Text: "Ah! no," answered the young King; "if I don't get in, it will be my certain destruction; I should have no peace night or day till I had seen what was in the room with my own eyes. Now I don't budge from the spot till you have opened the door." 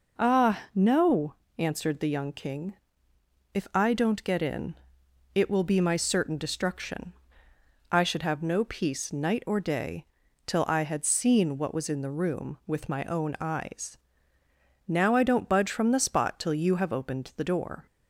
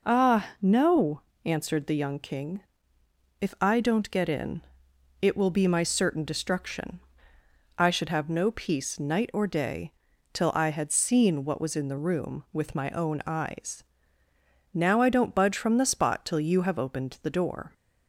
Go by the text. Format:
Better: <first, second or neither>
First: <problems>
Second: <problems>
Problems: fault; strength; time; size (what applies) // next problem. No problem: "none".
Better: neither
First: pauses between "day" and "till"; at 10.0 s; 0.40 s long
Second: pauses between "day" and "till"; at 9.9 s; 0.40 s long